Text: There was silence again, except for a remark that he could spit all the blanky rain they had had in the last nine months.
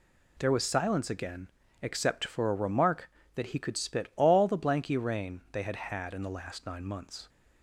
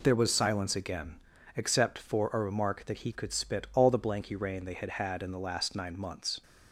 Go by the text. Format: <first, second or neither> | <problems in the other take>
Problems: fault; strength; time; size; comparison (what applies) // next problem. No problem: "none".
neither | none